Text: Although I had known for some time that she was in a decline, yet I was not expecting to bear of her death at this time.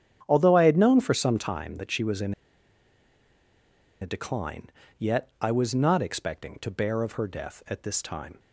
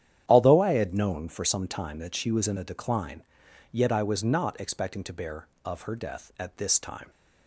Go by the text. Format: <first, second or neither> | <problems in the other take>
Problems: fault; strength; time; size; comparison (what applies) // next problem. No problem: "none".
second | starts louder than the rest; strong; until 1.2 s; 9 dB; strong in the second // pauses between "in" and "a"; strong; at 2.3 s; 1.6 s long